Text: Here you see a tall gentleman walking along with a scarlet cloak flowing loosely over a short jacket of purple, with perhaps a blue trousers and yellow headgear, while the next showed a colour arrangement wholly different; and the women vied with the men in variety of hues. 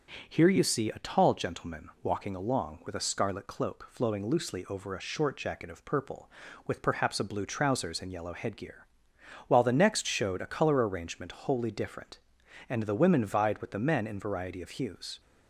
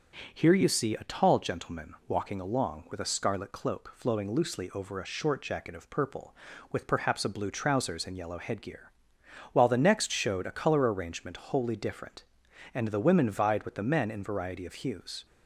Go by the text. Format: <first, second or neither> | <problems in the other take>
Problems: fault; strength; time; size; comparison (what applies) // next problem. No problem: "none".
neither | starts louder than the rest; the same in both